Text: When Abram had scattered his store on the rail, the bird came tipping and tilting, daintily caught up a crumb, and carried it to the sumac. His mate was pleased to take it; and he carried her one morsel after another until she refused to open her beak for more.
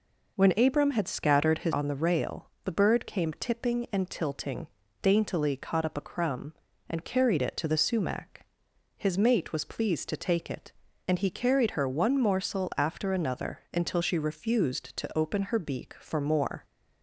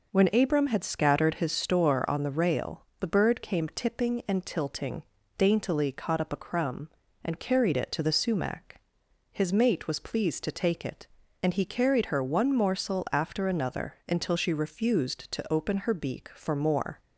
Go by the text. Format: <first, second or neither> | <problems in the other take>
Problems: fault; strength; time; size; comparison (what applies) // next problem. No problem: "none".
second | skips "store"; at 1.7 s